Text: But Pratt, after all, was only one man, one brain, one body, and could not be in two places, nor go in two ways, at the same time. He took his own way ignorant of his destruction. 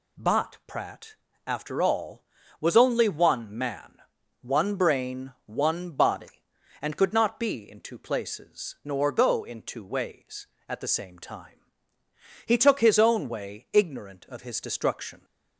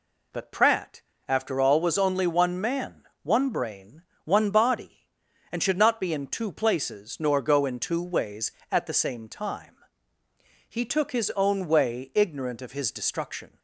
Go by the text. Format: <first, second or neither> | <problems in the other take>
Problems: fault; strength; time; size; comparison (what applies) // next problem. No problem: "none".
first | says "should" for "could"; at 5.6 s